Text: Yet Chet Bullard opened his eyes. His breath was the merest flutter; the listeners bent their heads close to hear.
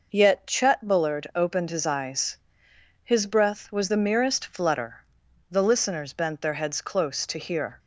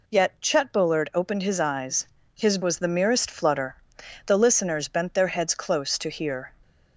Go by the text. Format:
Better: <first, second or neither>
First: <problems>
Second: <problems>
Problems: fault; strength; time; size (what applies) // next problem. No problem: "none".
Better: first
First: none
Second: skips "breath"; at 2.6 s